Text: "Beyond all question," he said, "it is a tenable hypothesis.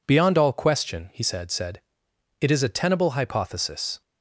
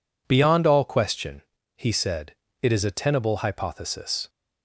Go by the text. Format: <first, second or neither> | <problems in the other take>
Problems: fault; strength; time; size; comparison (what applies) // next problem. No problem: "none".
second | says "said" twice; at 1.4 s